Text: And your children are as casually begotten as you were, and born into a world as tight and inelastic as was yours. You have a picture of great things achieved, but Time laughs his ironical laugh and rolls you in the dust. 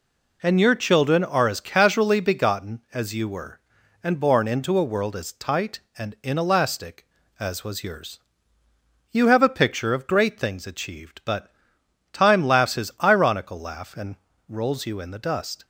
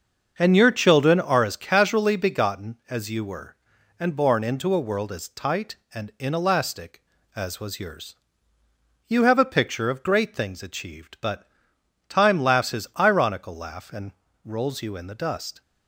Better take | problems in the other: first | starts louder than the rest; until 1.6 s; 6.5 dB // pauses between "but" and "Time"; noticeable; at 11.4 s; 0.62 s long; noticeable in the first // pauses between "and" and "rolls"; slight; at 14.1 s; 0.34 s long; slight in the first

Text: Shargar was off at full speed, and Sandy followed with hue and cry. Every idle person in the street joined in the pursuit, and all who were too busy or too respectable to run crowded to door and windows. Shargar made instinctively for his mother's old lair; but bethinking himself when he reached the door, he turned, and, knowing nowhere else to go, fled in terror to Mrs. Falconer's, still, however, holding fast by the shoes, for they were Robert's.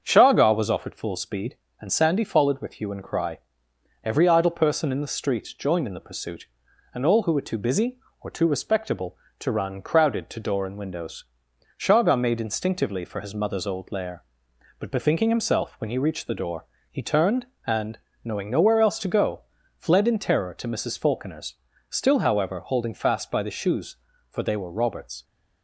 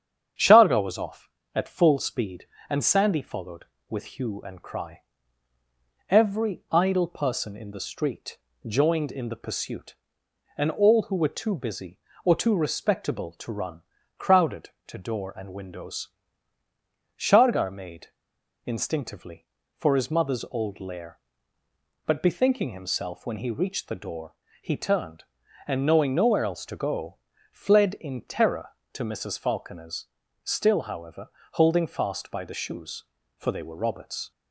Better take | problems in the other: first | starts louder than the rest; strong; until 1.6 s; 8 dB; strong in the first // pauses between "street" and "joined"; slight; at 8.3 s; 0.28 s long // pauses between "run" and "crowded"; at 13.8 s; 0.38 s long // pauses between "made" and "instinctively"; noticeable; at 18.0 s; 0.57 s long

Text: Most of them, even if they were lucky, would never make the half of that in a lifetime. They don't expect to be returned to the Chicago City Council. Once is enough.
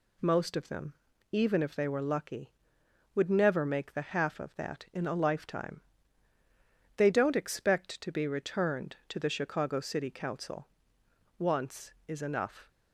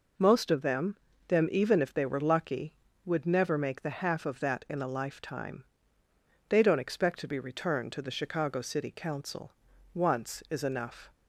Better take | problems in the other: first | says "them" twice; at 1.2 s

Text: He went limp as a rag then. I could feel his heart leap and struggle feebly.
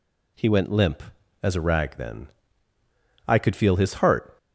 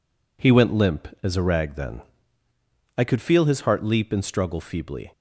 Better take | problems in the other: second | stops before "leap and struggle feebly"; at 4.3 s

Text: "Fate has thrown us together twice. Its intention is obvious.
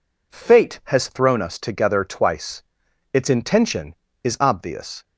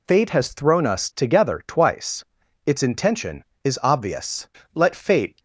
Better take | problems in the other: first | goes on to say "Let Fate"; noticeable; from 4.7 s on; 0.66 s long

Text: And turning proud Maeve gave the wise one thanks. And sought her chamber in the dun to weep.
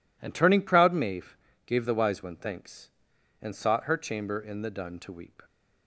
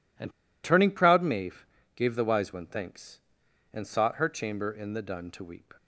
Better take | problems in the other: first | pauses between "And" and "turning"; slight; at 0.3 s; 0.32 s long // pauses between "Maeve" and "gave"; slight; at 1.6 s; 0.30 s long; slight in the first

